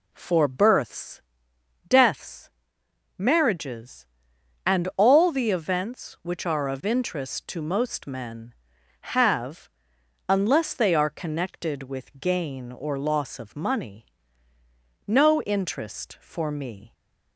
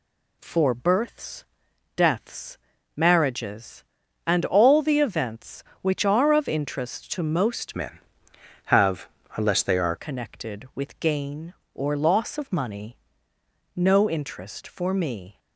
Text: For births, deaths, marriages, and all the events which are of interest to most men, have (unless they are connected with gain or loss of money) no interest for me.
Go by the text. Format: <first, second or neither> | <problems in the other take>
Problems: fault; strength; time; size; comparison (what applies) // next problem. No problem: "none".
first | changes voice from "men" to "are"; from 7.7 to 9.9 s; 2.2 s long